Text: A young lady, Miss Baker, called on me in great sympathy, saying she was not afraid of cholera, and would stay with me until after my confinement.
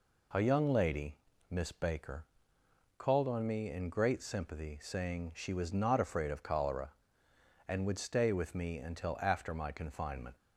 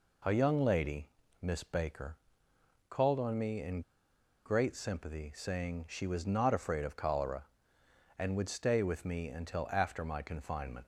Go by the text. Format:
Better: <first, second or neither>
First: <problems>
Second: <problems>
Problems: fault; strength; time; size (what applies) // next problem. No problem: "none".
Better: first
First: none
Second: pauses between "in" and "great"; noticeable; at 3.8 s; 0.64 s long